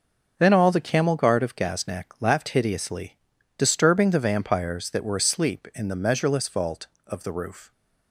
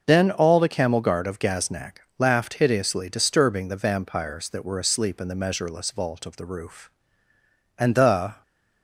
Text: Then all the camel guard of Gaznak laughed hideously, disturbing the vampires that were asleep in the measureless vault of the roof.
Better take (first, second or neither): first